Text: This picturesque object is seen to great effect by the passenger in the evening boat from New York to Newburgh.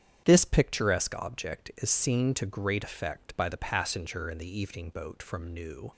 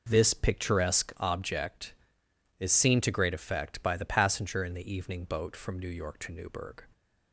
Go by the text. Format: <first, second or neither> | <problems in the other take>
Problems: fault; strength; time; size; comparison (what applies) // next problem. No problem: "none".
second | starts louder than the rest; strong; until 1.2 s; 8 dB // stops before "York to Newburgh"; at 5.9 s